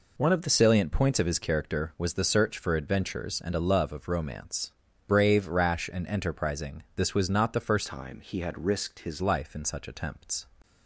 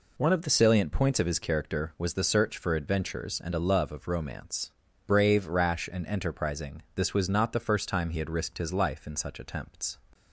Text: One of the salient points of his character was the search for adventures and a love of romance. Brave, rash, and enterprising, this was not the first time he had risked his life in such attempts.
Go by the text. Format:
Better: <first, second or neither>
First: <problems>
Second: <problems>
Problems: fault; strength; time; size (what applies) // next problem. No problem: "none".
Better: second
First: changes voice from "time" to "his"; from 7.8 to 9.2 s; 1.4 s long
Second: none